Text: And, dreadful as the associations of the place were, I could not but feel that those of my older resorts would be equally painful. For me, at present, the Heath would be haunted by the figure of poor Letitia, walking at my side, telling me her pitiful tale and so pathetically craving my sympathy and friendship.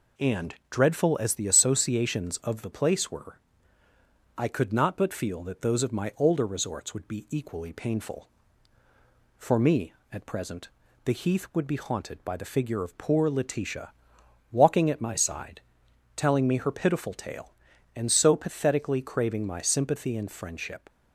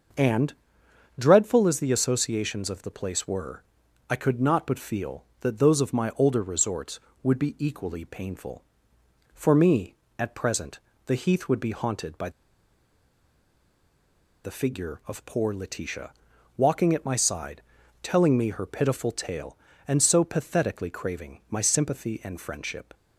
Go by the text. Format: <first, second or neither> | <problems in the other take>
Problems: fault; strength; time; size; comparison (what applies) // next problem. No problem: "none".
first | starts louder than the rest; until 1.8 s; 6.5 dB // pauses between "by" and "the"; strong; at 12.2 s; 2.1 s long